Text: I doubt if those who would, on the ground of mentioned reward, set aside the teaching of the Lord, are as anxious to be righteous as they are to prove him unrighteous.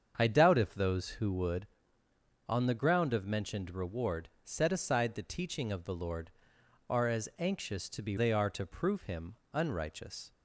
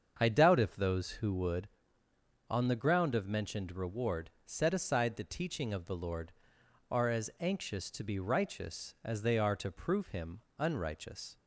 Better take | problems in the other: second | starts louder than the rest; strong; until 1.1 s; 7 dB; also in the second // skips "righteous as"; at 8.1 s // pauses between "him" and "unrighteous"; slight; at 9.3 s; 0.18 s long; slight in the second

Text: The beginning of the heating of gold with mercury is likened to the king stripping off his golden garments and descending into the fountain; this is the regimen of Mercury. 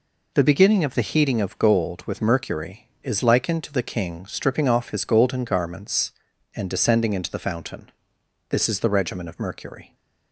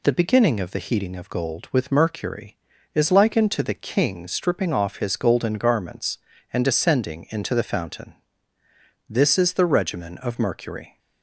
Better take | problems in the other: neither | none

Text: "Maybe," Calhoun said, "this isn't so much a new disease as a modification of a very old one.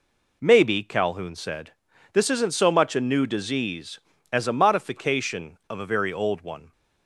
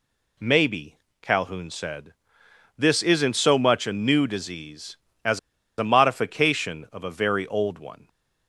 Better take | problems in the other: first | pauses between "as" and "a"; at 5.3 s; 0.38 s long

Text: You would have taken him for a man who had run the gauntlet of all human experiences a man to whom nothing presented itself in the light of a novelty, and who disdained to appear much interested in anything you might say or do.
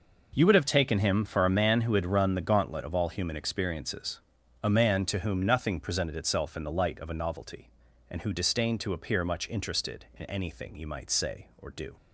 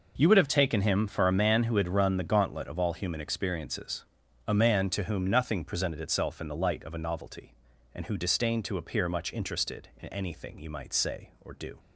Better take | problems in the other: neither | pauses between "experiences" and "a"; the same in both

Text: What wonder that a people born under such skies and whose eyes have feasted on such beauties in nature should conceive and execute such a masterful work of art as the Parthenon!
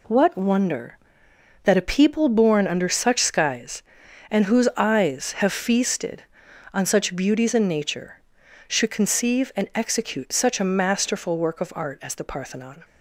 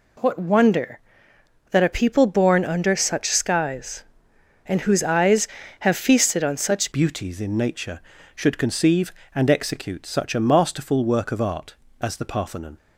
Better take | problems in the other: first | changes voice at "beauties"; from 6.9 s on; 5.8 s long

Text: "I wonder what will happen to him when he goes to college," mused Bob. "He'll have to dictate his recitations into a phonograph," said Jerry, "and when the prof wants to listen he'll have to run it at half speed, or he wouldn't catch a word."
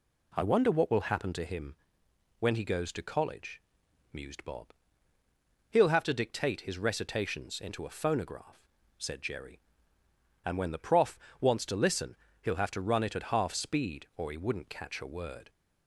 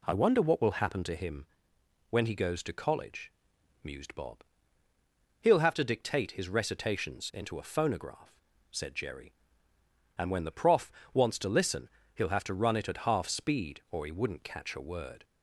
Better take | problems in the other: neither | pauses between "him" and "when"; noticeable; the same in both // pauses between "prof" and "wants"; slight; the same in both // pauses between "listen" and "he'll"; slight; the same in both

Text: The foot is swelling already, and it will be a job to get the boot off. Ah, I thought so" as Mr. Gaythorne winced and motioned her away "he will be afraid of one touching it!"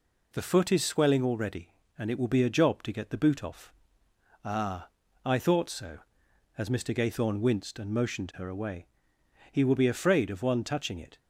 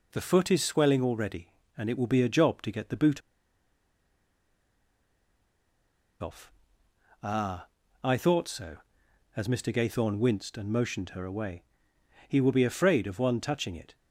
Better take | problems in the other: first | pauses between "boot" and "off"; strong; at 3.2 s; 3.0 s long // pauses between "away" and "he"; noticeable; at 11.6 s; 0.64 s long; noticeable in the first

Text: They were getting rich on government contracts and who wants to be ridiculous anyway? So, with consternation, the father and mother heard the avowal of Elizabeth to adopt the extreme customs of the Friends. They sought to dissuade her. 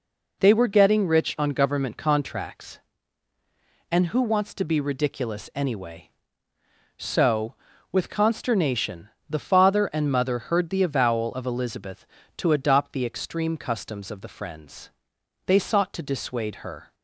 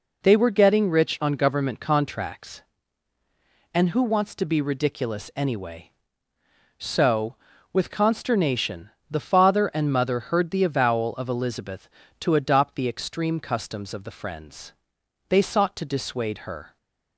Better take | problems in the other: neither | none

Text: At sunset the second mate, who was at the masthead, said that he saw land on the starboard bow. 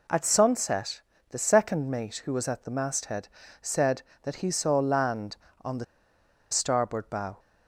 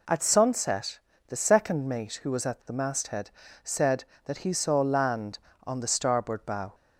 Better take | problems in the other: second | pauses between "sunset" and "the"; slight; at 1.0 s; 0.30 s long; slight in the second // pauses between "the" and "starboard"; noticeable; at 5.8 s; 0.67 s long

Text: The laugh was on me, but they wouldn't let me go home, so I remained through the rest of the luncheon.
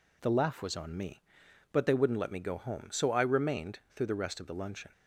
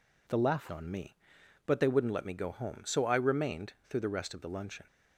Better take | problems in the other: first | skips "was"; at 0.6 s // pauses between "remained" and "through"; slight; at 3.7 s; 0.16 s long; slight in the first

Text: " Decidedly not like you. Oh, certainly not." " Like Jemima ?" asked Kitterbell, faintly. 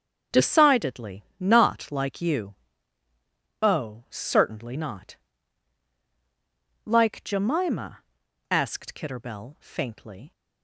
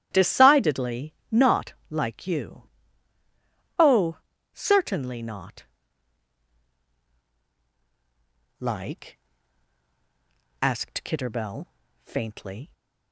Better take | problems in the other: first | starts louder than the rest; strong; until 1.1 s; 14.5 dB; strong in the first // pauses between "Decidedly" and "not"; slight; at 1.1 s; 0.16 s long; slight in the first // pauses between "not" and "like"; slight; at 1.7 s; 0.16 s long // skips "Jemima"; at 9.5 s

